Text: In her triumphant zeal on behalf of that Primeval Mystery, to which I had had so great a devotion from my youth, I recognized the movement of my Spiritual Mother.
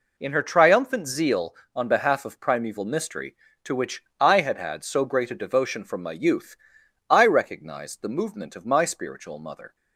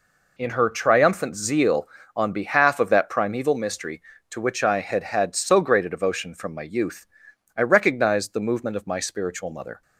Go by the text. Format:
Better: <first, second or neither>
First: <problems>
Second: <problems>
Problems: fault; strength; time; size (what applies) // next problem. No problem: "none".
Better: second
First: skips "that"; at 2.4 s // pauses between "which" and "I"; slight; at 4.0 s; 0.16 s long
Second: none